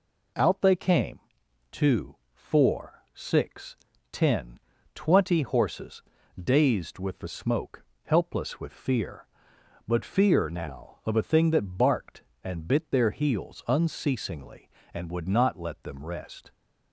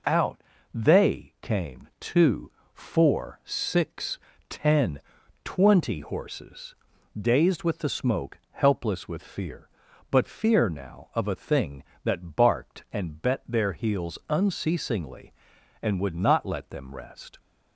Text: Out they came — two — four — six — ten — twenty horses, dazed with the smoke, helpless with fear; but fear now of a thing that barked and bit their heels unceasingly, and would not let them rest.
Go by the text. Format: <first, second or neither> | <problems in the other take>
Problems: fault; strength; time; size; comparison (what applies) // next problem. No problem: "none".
first | pauses between "Out" and "they"; slight; at 0.4 s; 0.30 s long // says "bet" for "bit"; at 13.2 s